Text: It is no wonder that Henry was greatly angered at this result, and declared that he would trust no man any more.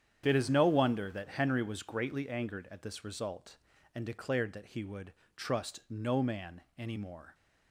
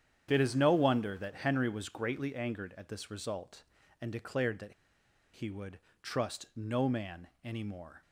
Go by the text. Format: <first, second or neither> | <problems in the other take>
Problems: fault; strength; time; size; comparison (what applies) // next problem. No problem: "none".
first | starts louder than the rest; strong; until 1.3 s; 9 dB; strong in the first // pauses between "that" and "he"; noticeable; at 4.7 s; 0.60 s long // pauses between "would" and "trust"; slight; at 5.7 s; 0.24 s long; slight in the first // pauses between "man" and "any"; slight; at 7.2 s; 0.16 s long; slight in the first